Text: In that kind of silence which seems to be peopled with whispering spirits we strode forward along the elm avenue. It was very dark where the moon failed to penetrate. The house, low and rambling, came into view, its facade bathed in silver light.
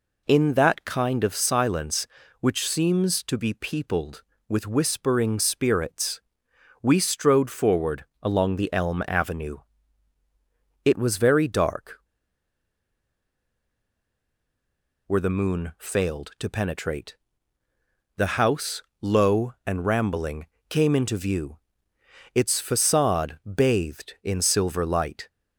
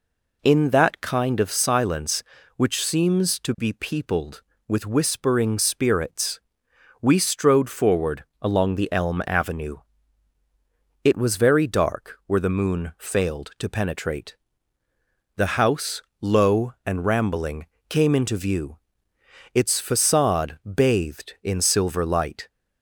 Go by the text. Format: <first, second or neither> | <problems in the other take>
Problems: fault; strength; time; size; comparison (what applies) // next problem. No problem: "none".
second | pauses between "spirits" and "we"; noticeable; at 6.2 s; 0.60 s long; noticeable in the second // pauses between "forward" and "along"; slight; at 8.0 s; 0.16 s long; slight in the second // pauses between "dark" and "where"; strong; at 11.9 s; 3.0 s long